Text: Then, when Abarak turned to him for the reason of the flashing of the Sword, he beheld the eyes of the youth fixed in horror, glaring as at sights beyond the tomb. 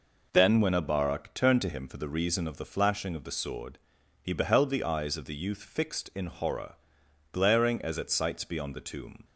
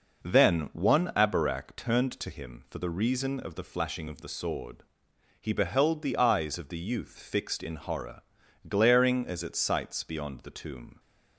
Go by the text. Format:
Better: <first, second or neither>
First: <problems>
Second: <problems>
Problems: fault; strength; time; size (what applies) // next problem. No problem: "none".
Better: first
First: none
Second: says "one" for "when"; at 0.7 s